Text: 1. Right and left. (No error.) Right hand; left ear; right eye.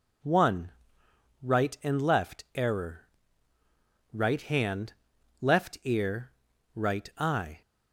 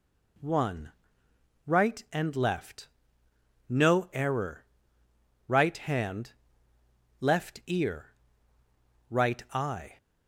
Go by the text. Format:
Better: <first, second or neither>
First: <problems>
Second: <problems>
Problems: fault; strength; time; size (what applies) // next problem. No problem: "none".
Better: second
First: skips "No"; at 2.4 s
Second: none